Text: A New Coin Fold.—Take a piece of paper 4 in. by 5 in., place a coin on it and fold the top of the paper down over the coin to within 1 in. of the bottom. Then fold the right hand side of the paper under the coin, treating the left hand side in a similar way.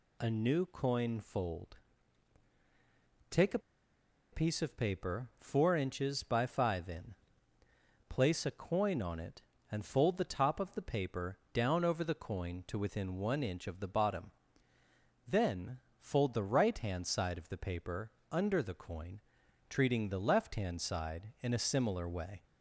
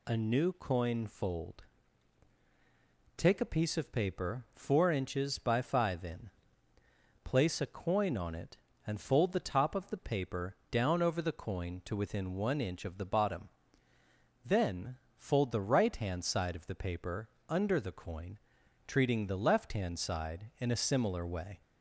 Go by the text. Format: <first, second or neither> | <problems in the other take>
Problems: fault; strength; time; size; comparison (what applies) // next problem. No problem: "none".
second | pauses between "a" and "piece"; noticeable; at 3.5 s; 0.74 s long // pauses between "Then" and "fold"; slight; at 15.7 s; 0.18 s long; slight in the second // pauses between "paper" and "under"; slight; at 18.1 s; 0.18 s long; slight in the second